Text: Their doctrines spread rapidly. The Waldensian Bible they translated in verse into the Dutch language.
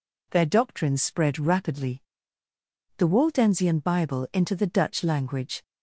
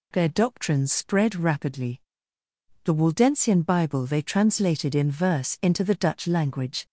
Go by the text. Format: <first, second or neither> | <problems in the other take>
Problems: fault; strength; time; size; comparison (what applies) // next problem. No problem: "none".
second | skips "they translated in verse"; at 4.3 s